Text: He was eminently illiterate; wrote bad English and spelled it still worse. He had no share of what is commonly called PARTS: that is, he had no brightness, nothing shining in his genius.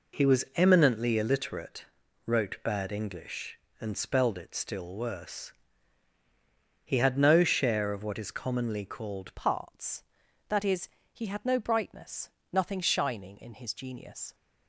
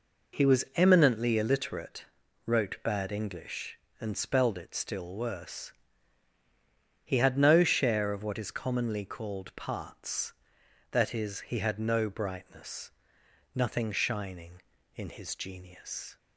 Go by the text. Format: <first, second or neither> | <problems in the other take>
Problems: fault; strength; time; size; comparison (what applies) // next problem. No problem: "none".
second | changes voice at "PARTS"; from 9.3 s on; 5.0 s long